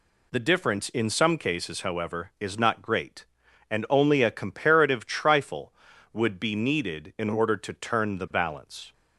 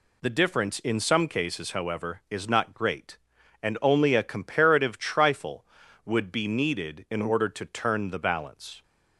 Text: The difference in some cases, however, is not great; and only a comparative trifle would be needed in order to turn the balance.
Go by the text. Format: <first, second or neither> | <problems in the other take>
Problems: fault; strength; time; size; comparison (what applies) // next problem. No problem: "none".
neither | none